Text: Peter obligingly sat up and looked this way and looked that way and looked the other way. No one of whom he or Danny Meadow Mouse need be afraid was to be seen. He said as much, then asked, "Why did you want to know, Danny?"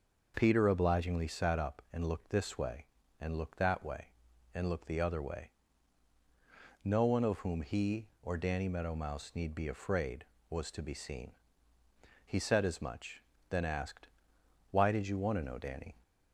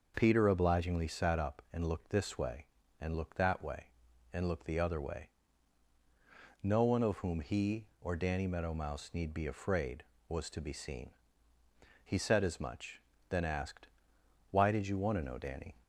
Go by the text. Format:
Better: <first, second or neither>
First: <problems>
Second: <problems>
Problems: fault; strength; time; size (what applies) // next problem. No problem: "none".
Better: neither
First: none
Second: none